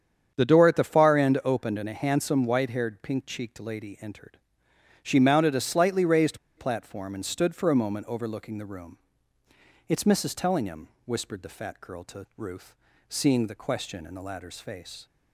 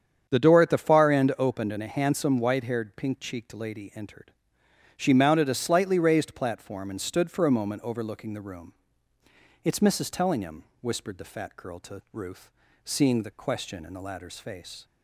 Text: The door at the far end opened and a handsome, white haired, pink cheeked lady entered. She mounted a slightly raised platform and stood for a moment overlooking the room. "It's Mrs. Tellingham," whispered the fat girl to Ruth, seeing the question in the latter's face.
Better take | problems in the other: second | starts louder than the rest; strong; until 1.3 s; 8 dB; strong in the second // pauses between "raised" and "platform"; slight; at 6.3 s; 0.20 s long

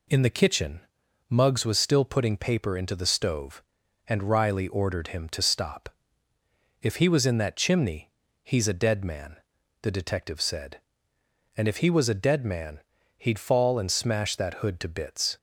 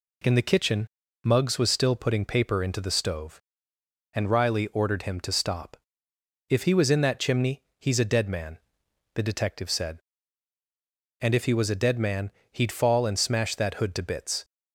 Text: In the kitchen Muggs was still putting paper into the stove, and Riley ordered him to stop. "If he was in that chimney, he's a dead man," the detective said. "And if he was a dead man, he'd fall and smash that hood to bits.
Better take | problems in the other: neither | pauses between "kitchen" and "Muggs"; the same in both

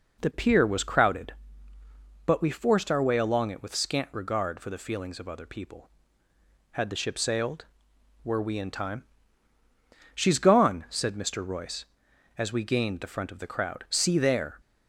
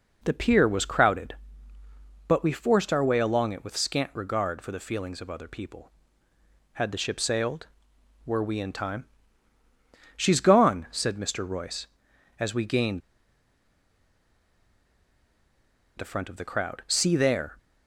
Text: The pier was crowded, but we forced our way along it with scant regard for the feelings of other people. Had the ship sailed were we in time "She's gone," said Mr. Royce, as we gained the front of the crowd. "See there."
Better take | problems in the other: first | pauses between "time" and "She's"; at 9.0 s; 1.1 s long; also in the first // pauses between "gained" and "the"; strong; at 13.0 s; 2.9 s long

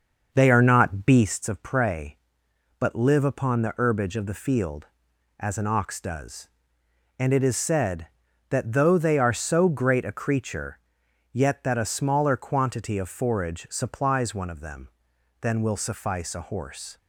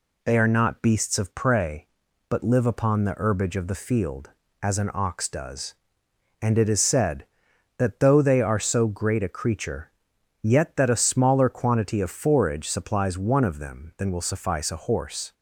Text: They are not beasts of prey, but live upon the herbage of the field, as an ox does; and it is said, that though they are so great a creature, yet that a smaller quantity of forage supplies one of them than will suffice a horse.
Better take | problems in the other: second | starts louder than the rest; until 1.3 s; 6.5 dB

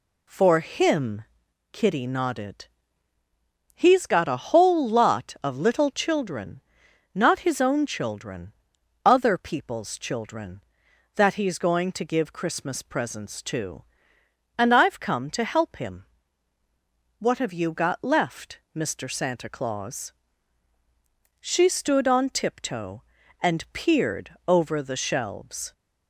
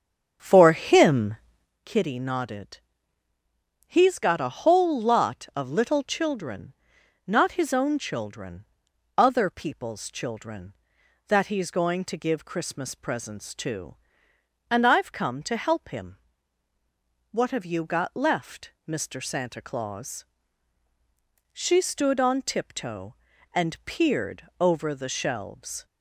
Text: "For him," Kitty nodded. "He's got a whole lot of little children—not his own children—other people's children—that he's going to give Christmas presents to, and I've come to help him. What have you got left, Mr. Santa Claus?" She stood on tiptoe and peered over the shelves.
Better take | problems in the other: first | starts louder than the rest; strong; until 1.9 s; 7.5 dB

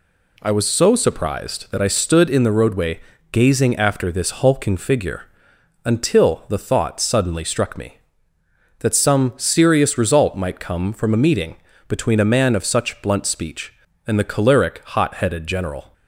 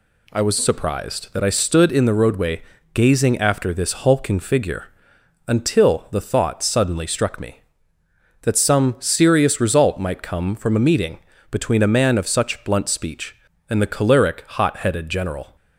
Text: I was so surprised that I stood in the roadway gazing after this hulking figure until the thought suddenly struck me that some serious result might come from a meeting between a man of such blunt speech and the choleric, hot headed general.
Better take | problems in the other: first | skips "so"; at 0.5 s // pauses between "roadway" and "gazing"; slight; at 2.6 s; 0.32 s long; slight in the first // pauses between "figure" and "until"; noticeable; at 4.8 s; 0.60 s long; noticeable in the first // pauses between "meeting" and "between"; slight; at 11.1 s; 0.32 s long; slight in the first

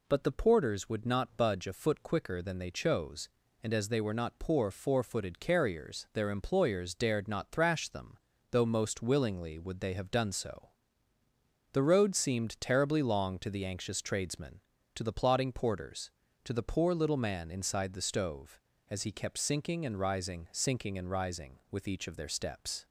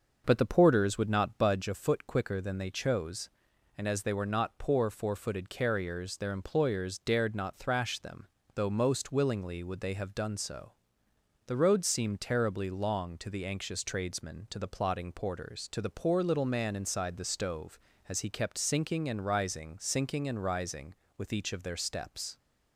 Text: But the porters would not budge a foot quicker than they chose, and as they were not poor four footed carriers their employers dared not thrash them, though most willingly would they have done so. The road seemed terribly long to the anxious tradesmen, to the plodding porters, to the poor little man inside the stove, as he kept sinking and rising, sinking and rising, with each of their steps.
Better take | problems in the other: first | starts louder than the rest; noticeable; until 1.6 s; 6 dB

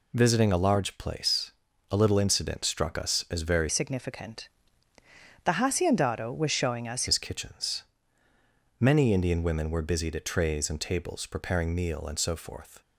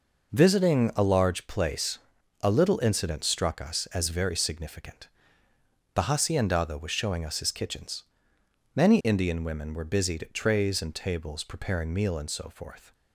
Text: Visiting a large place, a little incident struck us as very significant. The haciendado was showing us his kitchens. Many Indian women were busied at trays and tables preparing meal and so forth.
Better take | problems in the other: second | changes voice from "significant" to "us"; from 3.6 to 7.0 s; 3.4 s long

